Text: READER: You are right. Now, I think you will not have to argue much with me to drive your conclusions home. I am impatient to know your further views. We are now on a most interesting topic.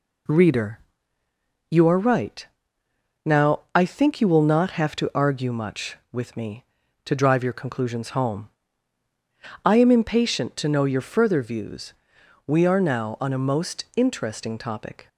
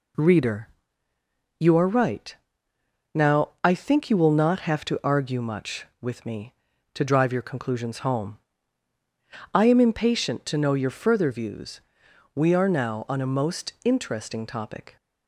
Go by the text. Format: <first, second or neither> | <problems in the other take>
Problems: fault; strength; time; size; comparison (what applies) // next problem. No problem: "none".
neither | none